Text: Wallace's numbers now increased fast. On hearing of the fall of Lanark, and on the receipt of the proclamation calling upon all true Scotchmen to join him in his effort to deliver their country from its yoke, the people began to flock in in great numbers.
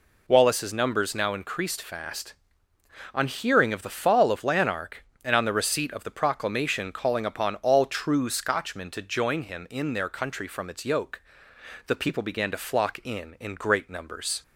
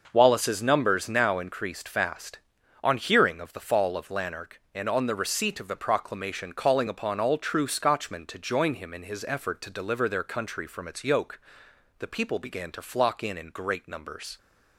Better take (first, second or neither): second